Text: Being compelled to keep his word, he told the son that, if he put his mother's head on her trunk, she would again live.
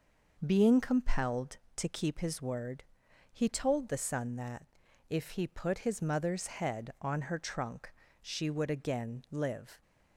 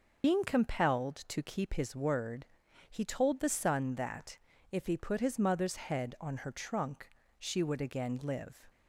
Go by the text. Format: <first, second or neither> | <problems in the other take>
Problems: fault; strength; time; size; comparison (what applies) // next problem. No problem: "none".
first | loses the start of "Being"; at 0.2 s; 90 ms